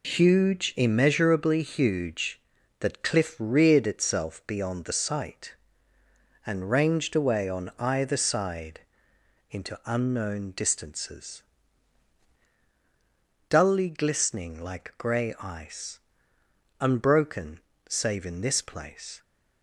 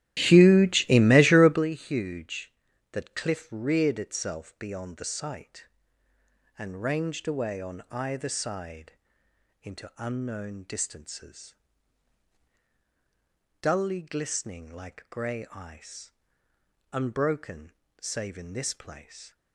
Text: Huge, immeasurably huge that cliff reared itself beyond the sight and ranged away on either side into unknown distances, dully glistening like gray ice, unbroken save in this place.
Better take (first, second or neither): first